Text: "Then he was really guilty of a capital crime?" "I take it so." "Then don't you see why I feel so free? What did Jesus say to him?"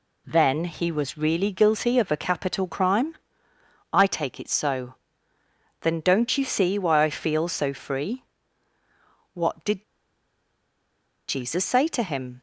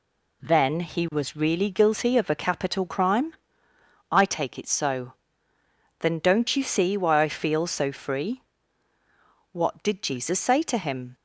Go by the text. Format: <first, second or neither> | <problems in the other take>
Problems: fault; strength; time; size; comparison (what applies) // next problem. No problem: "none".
second | pauses between "did" and "Jesus"; strong; at 9.8 s; 1.4 s long